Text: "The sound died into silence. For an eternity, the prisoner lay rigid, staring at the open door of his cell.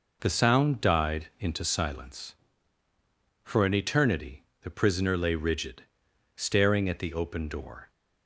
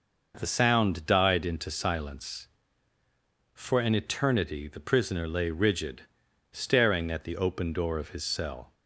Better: second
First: stops before "of his cell"; at 7.8 s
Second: none

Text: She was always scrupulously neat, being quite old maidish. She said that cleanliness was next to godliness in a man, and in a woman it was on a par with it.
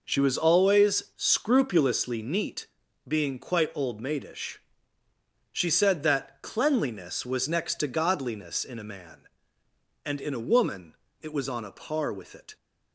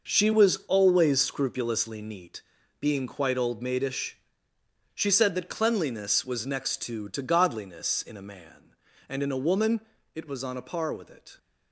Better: first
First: pauses between "woman" and "it"; slight; at 10.9 s; 0.26 s long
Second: says "to" twice; at 7.0 s // pauses between "woman" and "it"; slight; at 9.7 s; 0.34 s long

